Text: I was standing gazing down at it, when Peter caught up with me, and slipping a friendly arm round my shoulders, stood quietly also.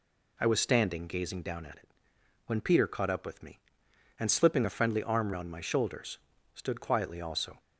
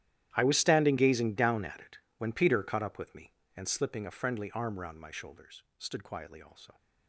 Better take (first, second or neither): first